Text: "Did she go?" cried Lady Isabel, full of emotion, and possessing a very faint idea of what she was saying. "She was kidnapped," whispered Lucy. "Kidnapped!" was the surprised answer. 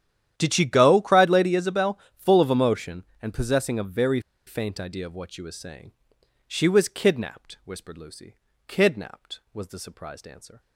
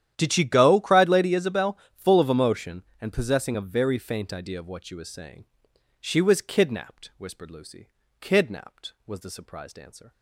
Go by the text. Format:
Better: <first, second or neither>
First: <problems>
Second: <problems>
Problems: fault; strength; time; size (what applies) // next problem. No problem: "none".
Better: second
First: starts louder than the rest; strong; until 1.3 s; 11 dB // pauses between "very" and "faint"; slight; at 4.1 s; 0.27 s long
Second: starts louder than the rest; strong; until 1.1 s; 11 dB